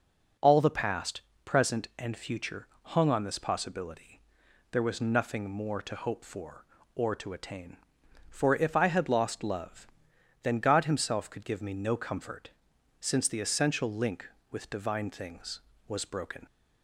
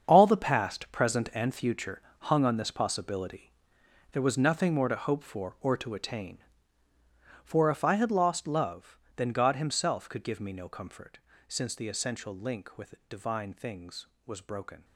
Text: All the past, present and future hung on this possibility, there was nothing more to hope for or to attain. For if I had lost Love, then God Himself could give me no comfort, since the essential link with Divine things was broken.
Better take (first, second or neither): first